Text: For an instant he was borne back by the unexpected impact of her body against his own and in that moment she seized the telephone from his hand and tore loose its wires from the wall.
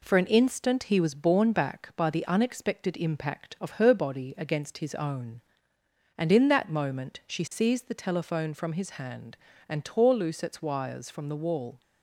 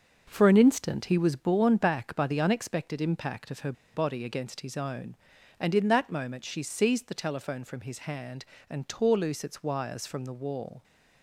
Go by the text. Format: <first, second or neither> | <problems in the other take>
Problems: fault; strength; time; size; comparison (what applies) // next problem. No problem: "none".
first | starts louder than the rest; noticeable; until 1.2 s; 6 dB // pauses between "her" and "body"; slight; at 3.7 s; 0.21 s long